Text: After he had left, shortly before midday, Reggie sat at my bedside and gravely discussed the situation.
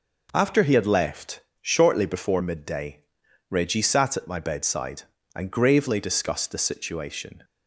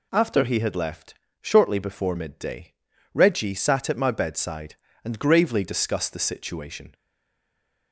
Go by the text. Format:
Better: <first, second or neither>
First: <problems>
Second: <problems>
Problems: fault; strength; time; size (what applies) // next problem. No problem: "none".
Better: first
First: none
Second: stays silent after the last word; from 6.9 s on; 1.0 s long